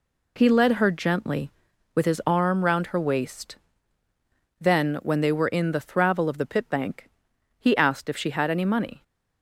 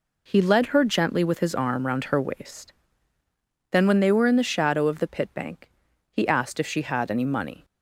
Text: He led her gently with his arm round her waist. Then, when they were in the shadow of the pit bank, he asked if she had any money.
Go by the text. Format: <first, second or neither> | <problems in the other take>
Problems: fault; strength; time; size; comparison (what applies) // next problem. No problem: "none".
second | says "thravel" for "shadow"; at 5.8 s